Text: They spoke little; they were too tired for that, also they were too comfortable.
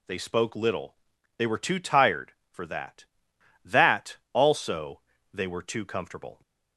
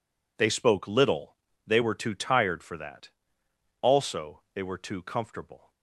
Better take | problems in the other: second | says "that" twice; at 3.6 s // pauses between "also" and "they"; slight; at 4.9 s; 0.34 s long

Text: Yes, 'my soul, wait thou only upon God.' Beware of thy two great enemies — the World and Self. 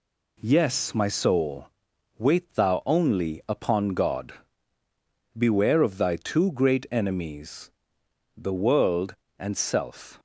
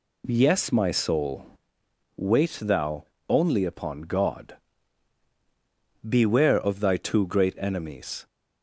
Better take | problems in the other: first | pauses between "thou" and "only"; slight; at 3.0 s; 0.26 s long // stops before "the World and Self"; at 8.2 s

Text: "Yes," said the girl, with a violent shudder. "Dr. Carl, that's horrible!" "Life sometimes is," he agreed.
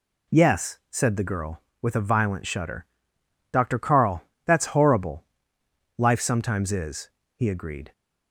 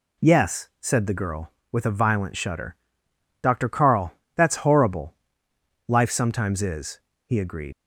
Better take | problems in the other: first | leaves "agreed" unfinished; at 7.7 s; 90 ms

